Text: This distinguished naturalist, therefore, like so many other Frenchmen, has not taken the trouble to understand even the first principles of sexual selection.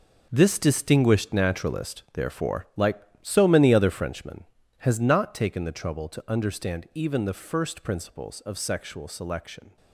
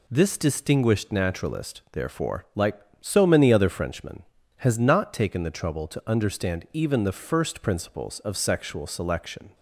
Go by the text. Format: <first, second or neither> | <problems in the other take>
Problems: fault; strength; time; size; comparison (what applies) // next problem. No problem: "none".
second | gets quieter; strong; throughout; 12.5 dB